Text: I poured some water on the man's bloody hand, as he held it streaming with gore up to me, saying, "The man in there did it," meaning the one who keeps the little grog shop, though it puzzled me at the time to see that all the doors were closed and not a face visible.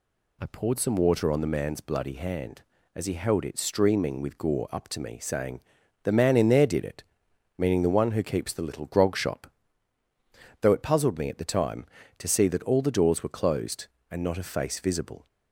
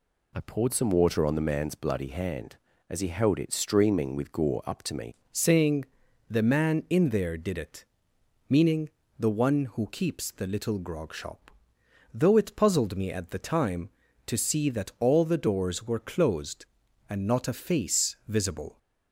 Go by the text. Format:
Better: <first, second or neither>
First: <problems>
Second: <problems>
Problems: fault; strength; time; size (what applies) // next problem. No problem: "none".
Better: first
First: none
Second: changes voice at "saying"; from 5.3 s on; 13.4 s long // pauses between "meaning" and "the"; slight; at 8.8 s; 0.28 s long